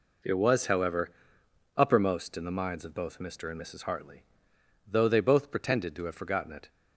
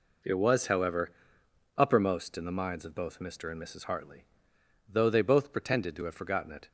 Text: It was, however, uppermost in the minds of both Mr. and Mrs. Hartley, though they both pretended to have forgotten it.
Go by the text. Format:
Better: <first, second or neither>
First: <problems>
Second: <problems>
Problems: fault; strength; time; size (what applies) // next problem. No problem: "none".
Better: neither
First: none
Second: none